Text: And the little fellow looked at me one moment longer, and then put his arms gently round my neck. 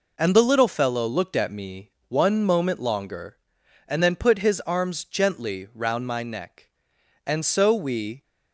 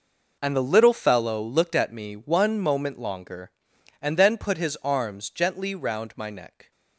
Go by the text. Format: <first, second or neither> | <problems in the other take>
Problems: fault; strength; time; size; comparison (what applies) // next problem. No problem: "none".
second | pauses between "me" and "one"; slight; at 1.9 s; 0.18 s long // goes on to say "And so we"; noticeable; from 7.2 s on; 0.98 s long